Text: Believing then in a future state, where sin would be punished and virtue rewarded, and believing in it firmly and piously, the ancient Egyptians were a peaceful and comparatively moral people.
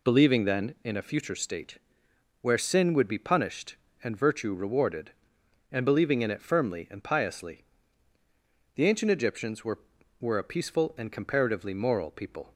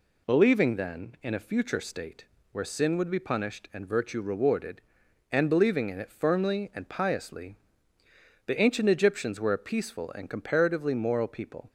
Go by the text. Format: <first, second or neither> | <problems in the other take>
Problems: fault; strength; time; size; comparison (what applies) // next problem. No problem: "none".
second | says "were" twice; at 10.2 s